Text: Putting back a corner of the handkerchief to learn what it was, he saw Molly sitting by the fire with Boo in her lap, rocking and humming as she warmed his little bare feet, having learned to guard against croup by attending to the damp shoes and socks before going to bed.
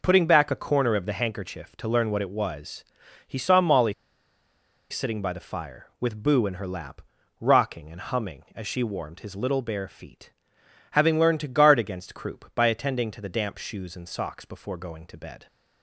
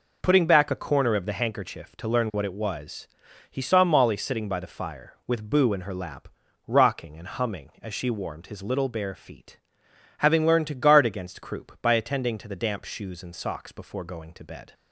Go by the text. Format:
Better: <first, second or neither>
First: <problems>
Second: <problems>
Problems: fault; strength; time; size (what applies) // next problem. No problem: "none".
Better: second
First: pauses between "Molly" and "sitting"; noticeable; at 3.9 s; 0.96 s long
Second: none